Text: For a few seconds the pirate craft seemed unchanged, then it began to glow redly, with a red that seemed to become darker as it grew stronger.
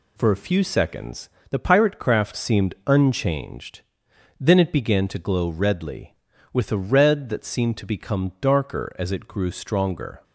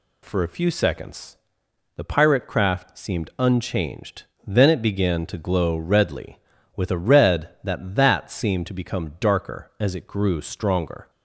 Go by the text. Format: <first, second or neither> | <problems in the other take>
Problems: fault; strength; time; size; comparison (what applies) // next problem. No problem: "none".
first | pauses between "seconds" and "the"; noticeable; at 1.3 s; 0.60 s long; slight in the first // says "that" twice; at 7.9 s